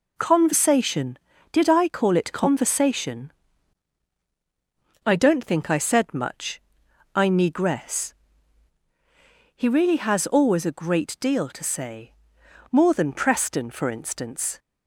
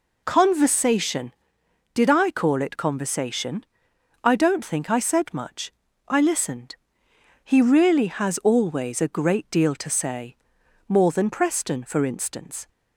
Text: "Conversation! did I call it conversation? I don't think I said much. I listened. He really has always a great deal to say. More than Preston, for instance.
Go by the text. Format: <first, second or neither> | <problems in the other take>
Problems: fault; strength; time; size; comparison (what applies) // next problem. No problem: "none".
second | says "negress" for "listened"; at 7.2 s